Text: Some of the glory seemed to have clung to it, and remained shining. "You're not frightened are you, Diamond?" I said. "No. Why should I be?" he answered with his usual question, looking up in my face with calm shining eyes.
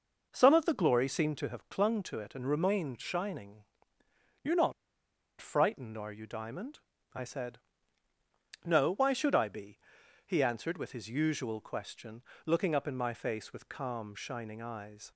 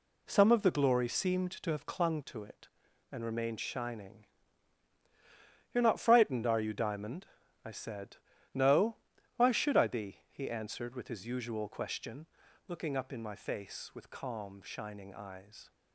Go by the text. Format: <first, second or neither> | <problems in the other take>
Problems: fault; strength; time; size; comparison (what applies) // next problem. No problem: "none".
second | pauses between "not" and "frightened"; noticeable; at 4.7 s; 0.67 s long